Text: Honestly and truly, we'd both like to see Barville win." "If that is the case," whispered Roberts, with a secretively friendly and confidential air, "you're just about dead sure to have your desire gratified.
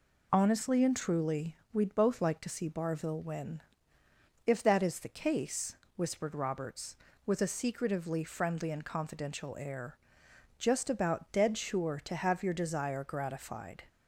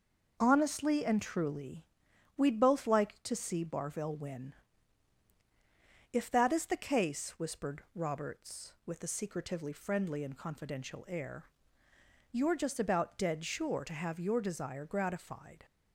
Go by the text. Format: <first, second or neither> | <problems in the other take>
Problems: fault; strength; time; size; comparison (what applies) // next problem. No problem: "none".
second | skips "you're"; at 10.2 s